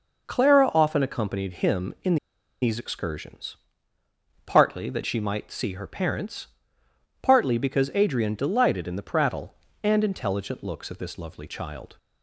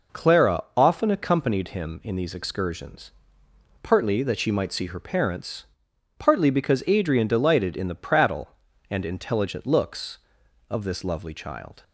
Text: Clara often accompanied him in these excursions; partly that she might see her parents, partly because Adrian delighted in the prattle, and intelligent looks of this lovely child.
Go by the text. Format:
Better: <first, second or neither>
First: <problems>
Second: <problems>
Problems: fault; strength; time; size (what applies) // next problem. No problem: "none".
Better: second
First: pauses between "in" and "these"; noticeable; at 2.1 s; 0.46 s long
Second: none